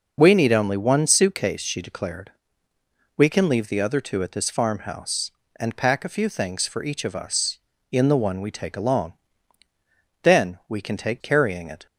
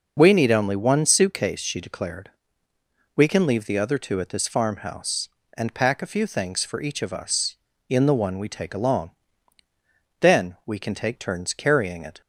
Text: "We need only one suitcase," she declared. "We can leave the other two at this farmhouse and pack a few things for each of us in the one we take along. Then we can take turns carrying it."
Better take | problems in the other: second | skips "turns"; at 11.2 s

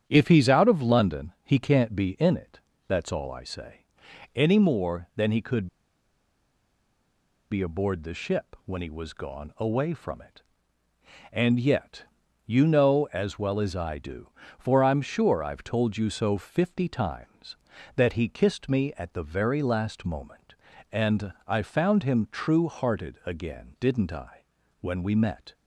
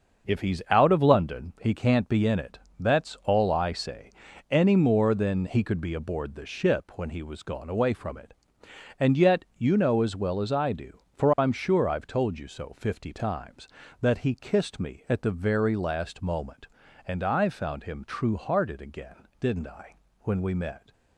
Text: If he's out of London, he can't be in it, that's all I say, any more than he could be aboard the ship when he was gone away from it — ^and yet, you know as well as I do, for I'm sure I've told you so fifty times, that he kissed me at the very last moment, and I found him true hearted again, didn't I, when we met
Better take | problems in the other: second | starts louder than the rest; strong; until 1.0 s; 9 dB; also in the second // pauses between "could" and "be"; strong; at 5.6 s; 1.8 s long // pauses between "and" and "I"; slight; at 21.3 s; 0.16 s long

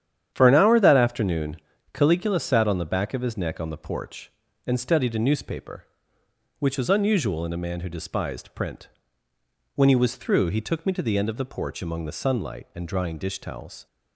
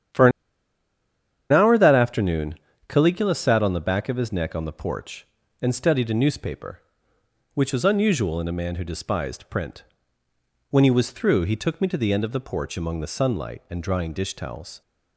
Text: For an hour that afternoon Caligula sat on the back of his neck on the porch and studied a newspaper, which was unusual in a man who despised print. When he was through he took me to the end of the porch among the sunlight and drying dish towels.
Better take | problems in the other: first | starts louder than the rest; strong; until 2.3 s; 9.5 dB; strong in the first // pauses between "an" and "hour"; at 0.3 s; 1.2 s long // pauses between "afternoon" and "Caligula"; slight; at 2.5 s; 0.34 s long; also in the first

